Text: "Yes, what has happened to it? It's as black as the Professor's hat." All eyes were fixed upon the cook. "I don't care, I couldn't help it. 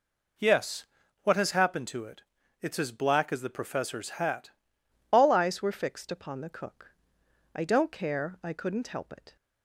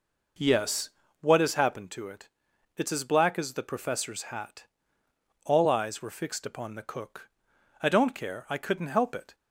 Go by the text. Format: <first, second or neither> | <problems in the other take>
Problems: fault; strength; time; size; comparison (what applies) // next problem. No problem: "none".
second | changes voice at "All"; from 5.1 s on; 4.2 s long